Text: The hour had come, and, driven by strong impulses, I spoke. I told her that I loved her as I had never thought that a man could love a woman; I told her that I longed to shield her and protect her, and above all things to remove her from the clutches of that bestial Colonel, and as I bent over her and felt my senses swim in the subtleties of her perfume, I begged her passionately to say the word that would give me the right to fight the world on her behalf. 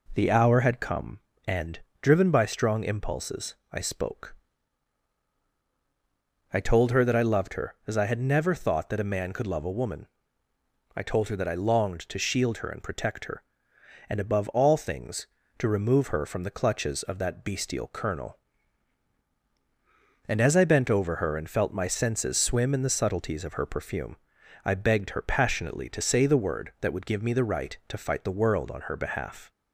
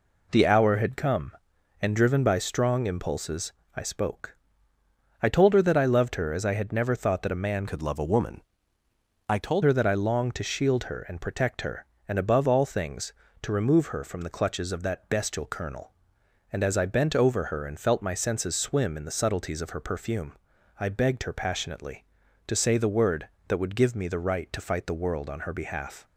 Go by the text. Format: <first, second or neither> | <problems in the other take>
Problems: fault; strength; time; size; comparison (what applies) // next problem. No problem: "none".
first | changes voice from "could" to "told"; from 7.6 to 9.6 s; 2.0 s long